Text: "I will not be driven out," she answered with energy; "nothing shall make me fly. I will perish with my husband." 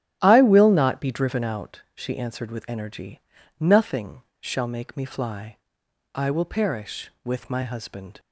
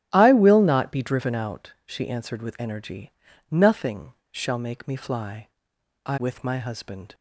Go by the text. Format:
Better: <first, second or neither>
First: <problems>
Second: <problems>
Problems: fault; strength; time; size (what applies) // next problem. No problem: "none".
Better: first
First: starts louder than the rest; strong; until 1.2 s; 9.5 dB // pauses between "nothing" and "shall"; slight; at 4.2 s; 0.20 s long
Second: starts louder than the rest; strong; until 1.1 s; 9.5 dB // pauses between "nothing" and "shall"; slight; at 4.1 s; 0.20 s long // skips "will perish"; at 6.1 s